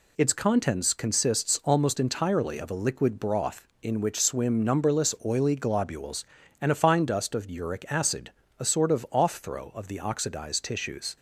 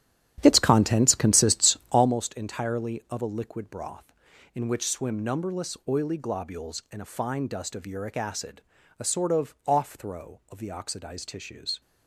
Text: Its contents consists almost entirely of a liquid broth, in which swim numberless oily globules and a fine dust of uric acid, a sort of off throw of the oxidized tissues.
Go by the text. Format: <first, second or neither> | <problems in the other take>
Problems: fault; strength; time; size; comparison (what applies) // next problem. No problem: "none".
first | starts louder than the rest; strong; until 2.2 s; 10 dB